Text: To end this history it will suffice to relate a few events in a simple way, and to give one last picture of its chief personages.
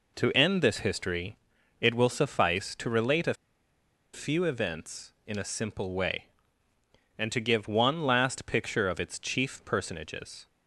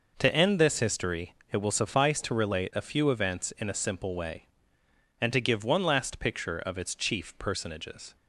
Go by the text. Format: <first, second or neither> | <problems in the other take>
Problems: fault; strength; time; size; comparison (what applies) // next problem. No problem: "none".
second | pauses between "history" and "it"; at 1.3 s; 0.44 s long; slight in the second // pauses between "a" and "few"; noticeable; at 3.3 s; 0.79 s long